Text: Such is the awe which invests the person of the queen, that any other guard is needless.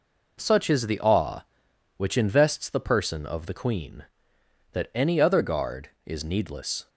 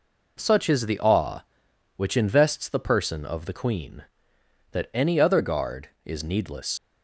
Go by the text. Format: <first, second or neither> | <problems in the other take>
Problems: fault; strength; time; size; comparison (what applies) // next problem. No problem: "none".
first | leaves "needless" unfinished; at 6.7 s; 105 ms